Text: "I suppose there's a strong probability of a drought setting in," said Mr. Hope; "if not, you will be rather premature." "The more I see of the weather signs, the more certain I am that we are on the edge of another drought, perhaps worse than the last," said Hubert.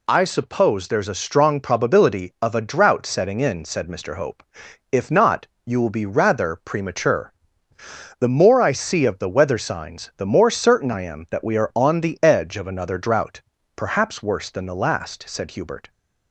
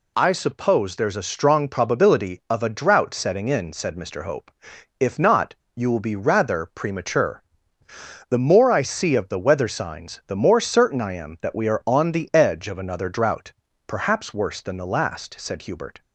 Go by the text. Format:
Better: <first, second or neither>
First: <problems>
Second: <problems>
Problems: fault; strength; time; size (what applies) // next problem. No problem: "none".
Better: neither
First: none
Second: none